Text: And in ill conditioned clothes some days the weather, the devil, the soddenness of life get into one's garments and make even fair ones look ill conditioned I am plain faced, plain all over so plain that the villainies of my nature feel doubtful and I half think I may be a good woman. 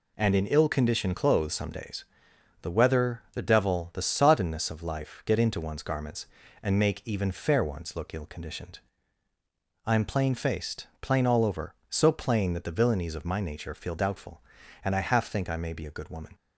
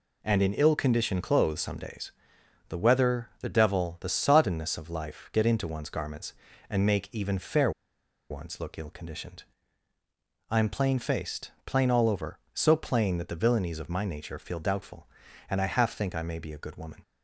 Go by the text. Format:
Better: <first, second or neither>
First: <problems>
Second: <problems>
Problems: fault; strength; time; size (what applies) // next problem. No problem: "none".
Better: first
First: pauses between "days" and "the"; noticeable; at 2.0 s; 0.58 s long // pauses between "conditioned" and "I"; at 8.7 s; 1.0 s long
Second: pauses between "days" and "the"; noticeable; at 2.1 s; 0.58 s long // pauses between "fair" and "ones"; noticeable; at 7.7 s; 0.59 s long // pauses between "conditioned" and "I"; at 9.4 s; 1.0 s long